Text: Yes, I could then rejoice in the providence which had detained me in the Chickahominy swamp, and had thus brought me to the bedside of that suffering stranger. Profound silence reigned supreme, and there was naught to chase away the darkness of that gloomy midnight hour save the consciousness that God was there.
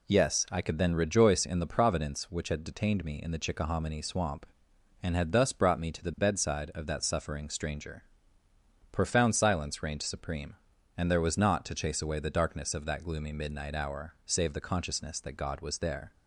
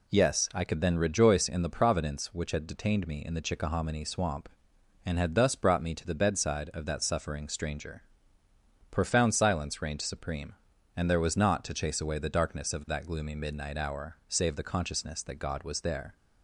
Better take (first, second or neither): neither